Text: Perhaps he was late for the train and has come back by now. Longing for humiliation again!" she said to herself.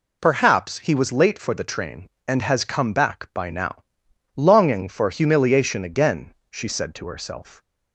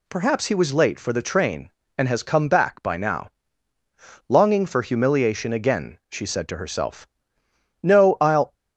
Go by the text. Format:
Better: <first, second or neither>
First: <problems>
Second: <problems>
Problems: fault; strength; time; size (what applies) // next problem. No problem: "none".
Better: first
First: none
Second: goes on to say "No I'll"; noticeable; from 7.8 s on; 0.72 s long